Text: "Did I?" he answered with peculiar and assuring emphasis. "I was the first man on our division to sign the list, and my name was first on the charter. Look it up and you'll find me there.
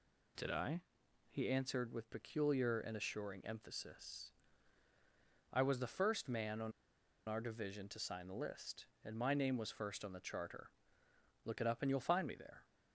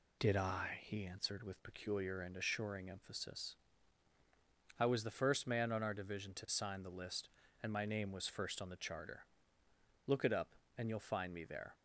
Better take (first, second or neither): second